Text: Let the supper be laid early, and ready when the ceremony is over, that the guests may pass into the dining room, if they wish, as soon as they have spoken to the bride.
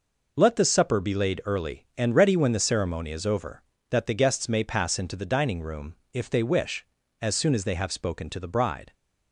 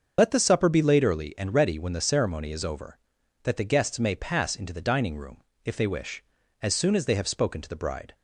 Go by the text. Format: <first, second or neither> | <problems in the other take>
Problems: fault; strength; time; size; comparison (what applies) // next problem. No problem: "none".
first | loses the start of "Let"; at 0.1 s; 40 ms // starts louder than the rest; until 1.1 s; 6.5 dB